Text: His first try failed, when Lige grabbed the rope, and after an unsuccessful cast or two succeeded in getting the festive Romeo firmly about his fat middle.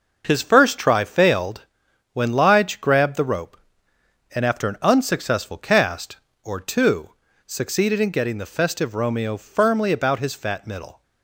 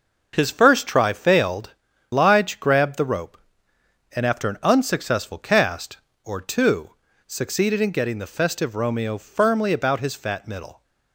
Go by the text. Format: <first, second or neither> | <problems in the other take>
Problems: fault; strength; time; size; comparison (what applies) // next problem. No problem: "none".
first | starts louder than the rest; noticeable; until 1.3 s; 6 dB // skips "when"; at 1.9 s // pauses between "two" and "succeeded"; slight; at 6.9 s; 0.36 s long; slight in the first